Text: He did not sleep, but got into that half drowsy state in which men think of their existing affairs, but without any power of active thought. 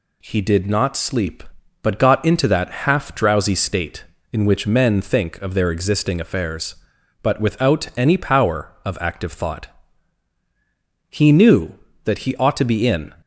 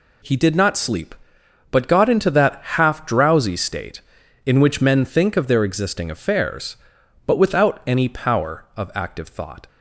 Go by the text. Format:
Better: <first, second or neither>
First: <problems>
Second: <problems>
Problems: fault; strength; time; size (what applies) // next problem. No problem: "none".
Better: second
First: goes on to say "He knew that he ought to be in"; strong; from 11.0 s on; 2.0 s long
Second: none